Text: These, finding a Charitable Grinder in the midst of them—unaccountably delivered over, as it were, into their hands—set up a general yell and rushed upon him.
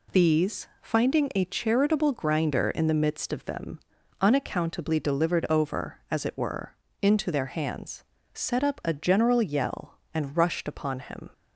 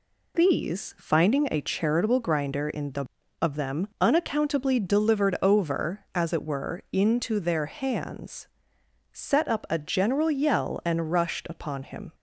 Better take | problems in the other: first | skips "midst"; at 3.2 s

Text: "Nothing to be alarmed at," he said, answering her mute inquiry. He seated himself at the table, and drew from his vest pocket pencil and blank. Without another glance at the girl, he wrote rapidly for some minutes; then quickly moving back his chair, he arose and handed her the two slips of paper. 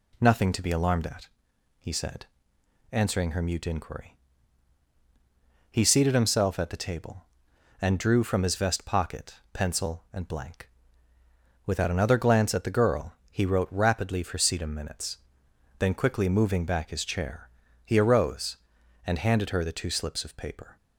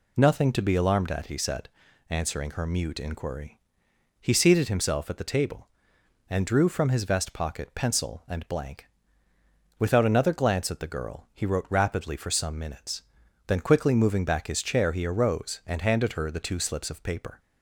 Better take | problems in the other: second | pauses between "pocket" and "pencil"; slight; at 9.3 s; 0.18 s long // says "sedum" for "some"; at 14.3 s

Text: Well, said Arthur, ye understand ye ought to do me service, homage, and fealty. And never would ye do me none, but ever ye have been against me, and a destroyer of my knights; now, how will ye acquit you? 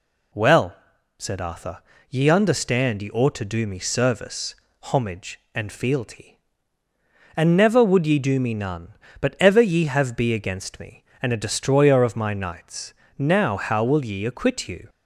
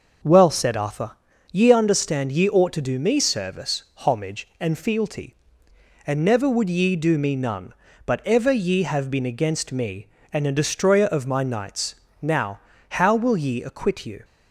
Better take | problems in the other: second | says "be" for "been"; at 10.1 s

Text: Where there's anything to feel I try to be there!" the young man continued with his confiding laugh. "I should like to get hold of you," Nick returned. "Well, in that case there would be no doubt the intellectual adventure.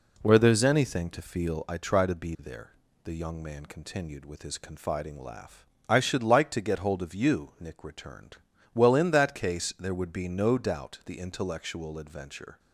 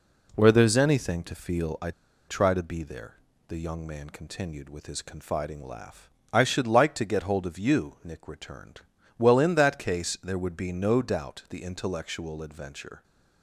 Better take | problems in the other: first | pauses between "I" and "try"; at 1.9 s; 0.37 s long

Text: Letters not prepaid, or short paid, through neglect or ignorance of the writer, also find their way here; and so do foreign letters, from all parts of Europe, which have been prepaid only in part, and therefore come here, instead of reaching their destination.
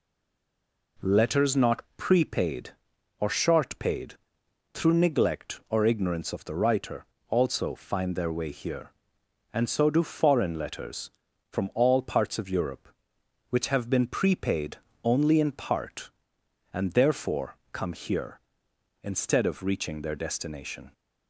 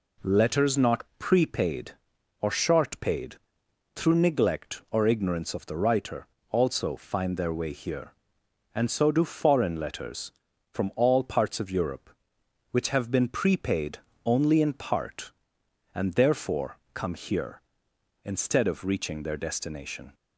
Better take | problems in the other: second | stays silent before the first word; slight; until 0.9 s; 0.9 s long // pauses between "not" and "prepaid"; slight; at 1.8 s; 0.16 s long; slight in the second // pauses between "prepaid" and "only"; slight; at 14.7 s; 0.28 s long; slight in the second // pauses between "therefore" and "come"; slight; at 17.5 s; 0.16 s long; slight in the second

